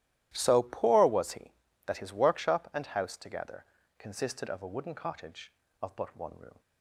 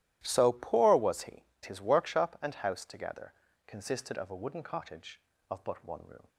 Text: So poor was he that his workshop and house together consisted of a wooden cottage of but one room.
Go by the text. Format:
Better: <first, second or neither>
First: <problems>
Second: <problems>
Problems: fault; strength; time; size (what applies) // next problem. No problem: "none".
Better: first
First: starts louder than the rest; strong; until 1.3 s; 14 dB // pauses between "together" and "consisted"; slight; at 3.6 s; 0.34 s long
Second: starts louder than the rest; strong; until 1.2 s; 13.5 dB // skips "that"; at 1.5 s // pauses between "together" and "consisted"; slight; at 3.3 s; 0.34 s long